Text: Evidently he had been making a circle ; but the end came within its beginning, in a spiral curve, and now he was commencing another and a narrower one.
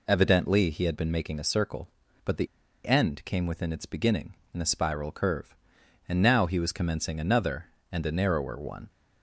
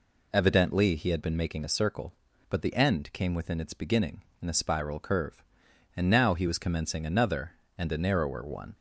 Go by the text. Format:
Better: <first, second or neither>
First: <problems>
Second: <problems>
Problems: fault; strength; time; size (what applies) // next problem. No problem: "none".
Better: second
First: pauses between "the" and "end"; at 2.4 s; 0.39 s long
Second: none